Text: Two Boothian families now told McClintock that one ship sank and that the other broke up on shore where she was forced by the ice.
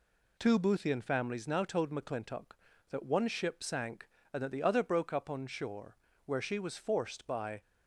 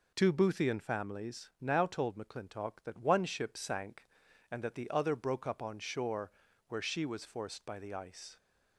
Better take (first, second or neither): second